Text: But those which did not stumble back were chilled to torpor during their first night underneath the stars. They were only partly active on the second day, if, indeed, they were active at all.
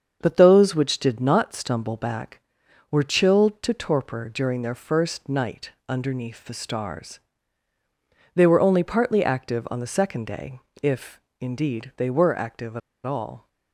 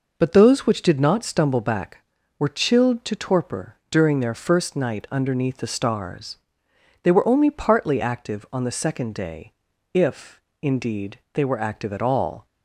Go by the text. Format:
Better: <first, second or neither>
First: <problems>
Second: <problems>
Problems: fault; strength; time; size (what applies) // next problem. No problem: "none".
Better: second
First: starts louder than the rest; until 1.2 s; 7 dB // pauses between "night" and "underneath"; slight; at 5.7 s; 0.16 s long // pauses between "at" and "all"; slight; at 12.8 s; 0.25 s long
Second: none